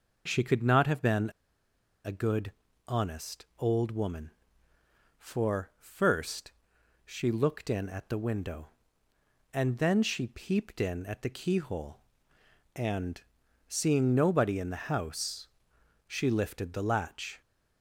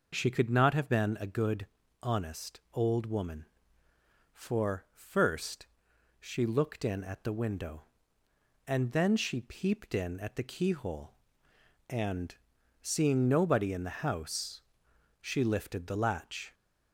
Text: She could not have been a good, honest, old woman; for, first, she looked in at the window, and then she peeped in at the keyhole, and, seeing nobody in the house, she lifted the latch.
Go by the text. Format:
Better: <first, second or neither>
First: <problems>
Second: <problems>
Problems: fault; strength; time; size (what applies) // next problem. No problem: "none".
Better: second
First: pauses between "been" and "a"; noticeable; at 1.3 s; 0.74 s long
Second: none